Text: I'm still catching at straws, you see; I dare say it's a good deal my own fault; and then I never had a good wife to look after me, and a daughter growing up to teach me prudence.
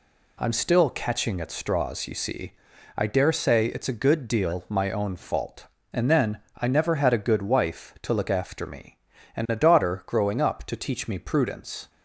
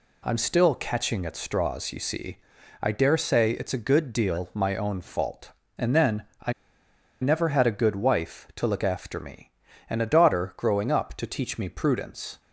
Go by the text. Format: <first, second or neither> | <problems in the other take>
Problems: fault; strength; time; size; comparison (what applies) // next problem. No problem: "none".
first | pauses between "then" and "I"; slight; at 6.2 s; 0.18 s long; slight in the first // pauses between "I" and "never"; noticeable; at 6.5 s; 0.68 s long